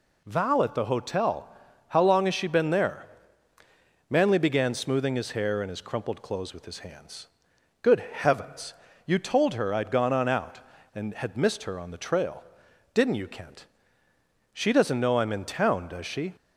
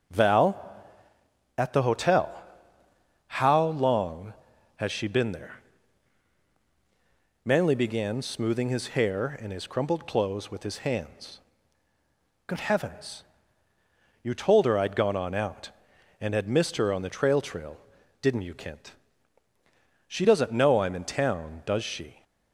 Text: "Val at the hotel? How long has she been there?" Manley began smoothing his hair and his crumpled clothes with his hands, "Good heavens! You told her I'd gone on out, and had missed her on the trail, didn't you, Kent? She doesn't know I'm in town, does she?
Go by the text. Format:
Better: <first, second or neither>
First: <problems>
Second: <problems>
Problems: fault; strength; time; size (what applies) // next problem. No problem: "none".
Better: first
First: none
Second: starts louder than the rest; strong; until 2.1 s; 7.5 dB // says "trail" twice; at 17.3 s